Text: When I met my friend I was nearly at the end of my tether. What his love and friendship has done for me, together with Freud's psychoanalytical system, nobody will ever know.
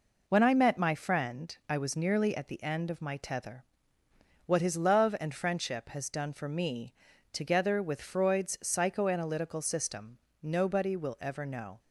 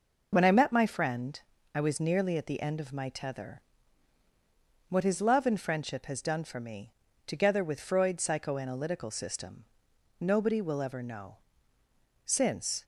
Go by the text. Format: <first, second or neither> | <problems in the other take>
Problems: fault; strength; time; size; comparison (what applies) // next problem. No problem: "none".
first | pauses between "friend" and "I"; slight; at 1.3 s; 0.36 s long // goes on to say "Since"; from 12.2 s on; 0.58 s long